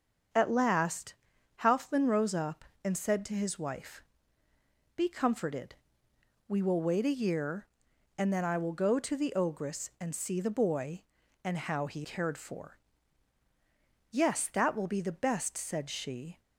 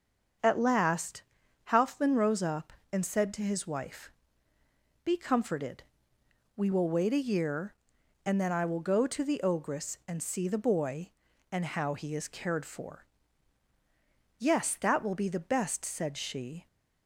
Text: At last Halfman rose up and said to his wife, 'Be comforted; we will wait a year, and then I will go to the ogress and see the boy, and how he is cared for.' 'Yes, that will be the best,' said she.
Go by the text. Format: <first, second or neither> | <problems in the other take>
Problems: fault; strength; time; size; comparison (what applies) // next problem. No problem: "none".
second | starts louder than the rest; until 1.8 s; 7 dB; also in the second // pauses between "last" and "Halfman"; noticeable; at 1.1 s; 0.48 s long; noticeable in the second // skips "is"; at 12.0 s